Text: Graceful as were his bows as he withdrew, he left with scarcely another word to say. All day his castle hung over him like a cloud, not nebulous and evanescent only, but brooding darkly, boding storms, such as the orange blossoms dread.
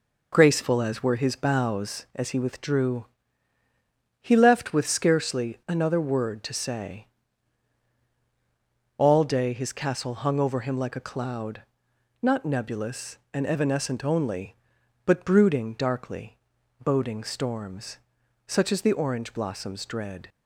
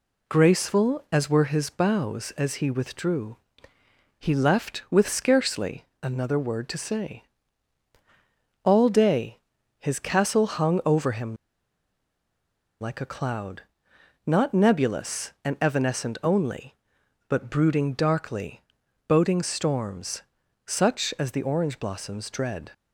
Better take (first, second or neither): first